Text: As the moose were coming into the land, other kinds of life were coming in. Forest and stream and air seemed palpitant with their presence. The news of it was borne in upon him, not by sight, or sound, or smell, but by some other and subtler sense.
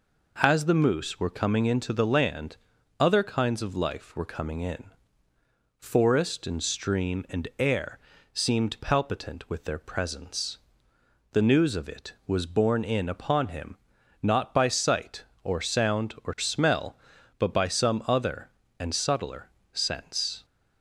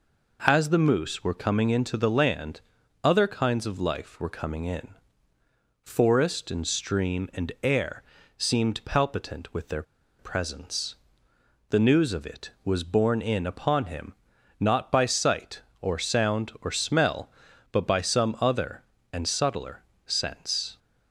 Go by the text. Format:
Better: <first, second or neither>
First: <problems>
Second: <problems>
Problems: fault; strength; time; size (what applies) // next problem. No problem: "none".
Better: first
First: pauses between "air" and "seemed"; slight; at 7.9 s; 0.36 s long // pauses between "subtler" and "sense"; slight; at 19.5 s; 0.22 s long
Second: pauses between "air" and "seemed"; slight; at 8.0 s; 0.36 s long // pauses between "their" and "presence"; slight; at 9.8 s; 0.36 s long // pauses between "subtler" and "sense"; slight; at 19.8 s; 0.22 s long